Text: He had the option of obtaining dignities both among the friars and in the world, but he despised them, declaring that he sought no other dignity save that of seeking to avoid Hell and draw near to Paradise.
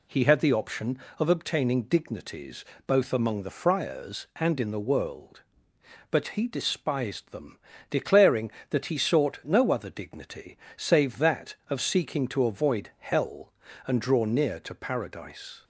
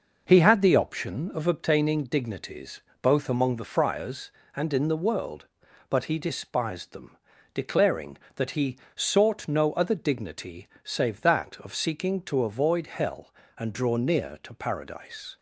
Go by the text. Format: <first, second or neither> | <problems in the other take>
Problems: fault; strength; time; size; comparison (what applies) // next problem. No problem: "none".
first | starts louder than the rest; noticeable; until 1.6 s; 5.5 dB // pauses between "dignities" and "both"; slight; at 2.8 s; 0.22 s long; slight in the first // pauses between "he" and "sought"; slight; at 8.7 s; 0.16 s long // pauses between "dignity" and "save"; slight; at 10.6 s; 0.16 s long; slight in the first